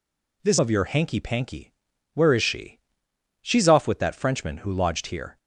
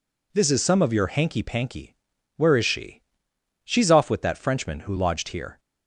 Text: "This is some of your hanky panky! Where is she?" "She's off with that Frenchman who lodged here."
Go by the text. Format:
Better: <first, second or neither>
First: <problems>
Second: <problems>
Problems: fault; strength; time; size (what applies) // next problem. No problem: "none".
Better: second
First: skips "is some"; at 0.5 s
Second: none